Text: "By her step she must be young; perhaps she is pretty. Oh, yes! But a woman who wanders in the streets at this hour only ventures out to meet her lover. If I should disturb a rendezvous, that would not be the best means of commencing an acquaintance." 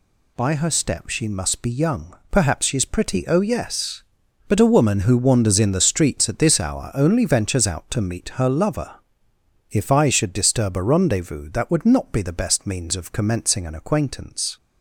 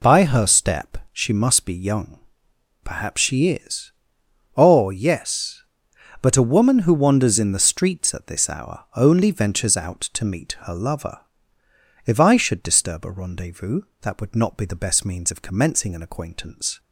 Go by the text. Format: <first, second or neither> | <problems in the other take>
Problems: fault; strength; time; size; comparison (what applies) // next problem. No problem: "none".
first | pauses between "step" and "she"; slight; at 0.9 s; 0.16 s long // skips "pretty"; at 4.2 s